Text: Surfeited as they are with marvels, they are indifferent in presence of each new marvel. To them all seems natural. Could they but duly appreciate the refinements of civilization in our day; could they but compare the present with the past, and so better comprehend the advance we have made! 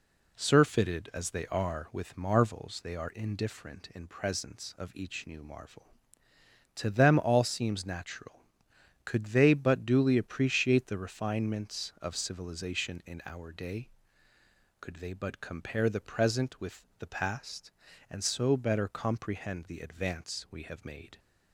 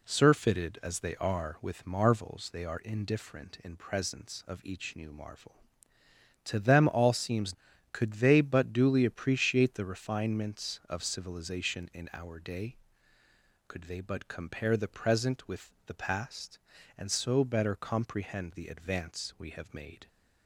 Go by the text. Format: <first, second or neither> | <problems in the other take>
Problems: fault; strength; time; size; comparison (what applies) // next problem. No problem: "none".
first | skips "natural"; at 7.7 s // pauses between "with" and "the"; slight; at 15.6 s; 0.16 s long; slight in the first